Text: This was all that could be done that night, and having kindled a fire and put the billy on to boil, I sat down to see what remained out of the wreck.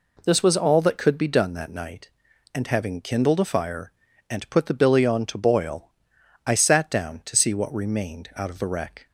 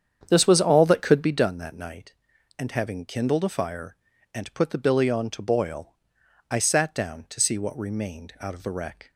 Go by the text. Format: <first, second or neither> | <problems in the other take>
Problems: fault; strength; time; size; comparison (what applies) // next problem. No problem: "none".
first | starts louder than the rest; strong; until 1.5 s; 8 dB